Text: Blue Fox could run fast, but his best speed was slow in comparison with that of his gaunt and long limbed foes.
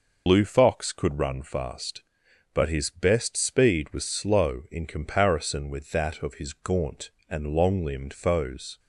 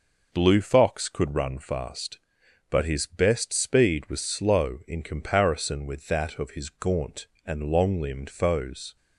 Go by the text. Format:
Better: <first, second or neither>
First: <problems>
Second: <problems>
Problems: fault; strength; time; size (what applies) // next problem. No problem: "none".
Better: second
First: loses the start of "Blue"; at 0.2 s; 90 ms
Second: none